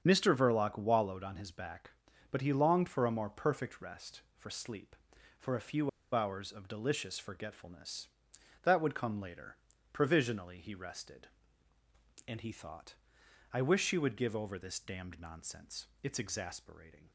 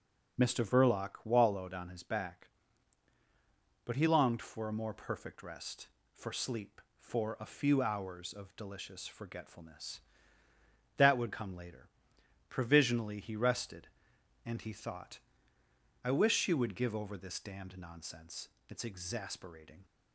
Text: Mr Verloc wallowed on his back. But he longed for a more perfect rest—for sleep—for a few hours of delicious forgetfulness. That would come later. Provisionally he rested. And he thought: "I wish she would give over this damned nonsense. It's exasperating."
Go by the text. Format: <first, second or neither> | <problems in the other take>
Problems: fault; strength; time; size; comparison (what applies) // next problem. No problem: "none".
second | starts louder than the rest; until 1.0 s; 7 dB; also in the second // pauses between "few" and "hours"; slight; at 5.8 s; 0.25 s long